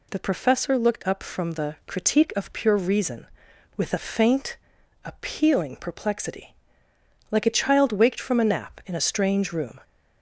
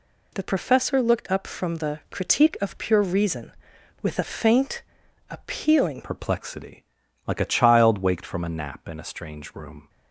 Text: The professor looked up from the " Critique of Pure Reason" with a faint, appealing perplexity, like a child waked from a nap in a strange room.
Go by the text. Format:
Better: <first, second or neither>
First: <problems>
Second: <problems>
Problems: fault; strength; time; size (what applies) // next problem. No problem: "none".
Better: first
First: none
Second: changes voice at "perplexity"; from 6.0 s on; 3.8 s long